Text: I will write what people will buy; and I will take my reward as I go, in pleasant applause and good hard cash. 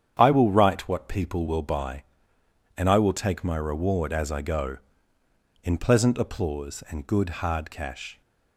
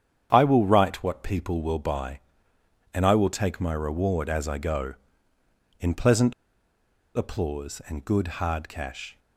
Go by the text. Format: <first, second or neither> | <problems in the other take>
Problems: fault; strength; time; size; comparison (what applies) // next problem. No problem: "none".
first | starts louder than the rest; strong; until 1.3 s; 8.5 dB; strong in the first // pauses between "pleasant" and "applause"; noticeable; at 6.3 s; 0.83 s long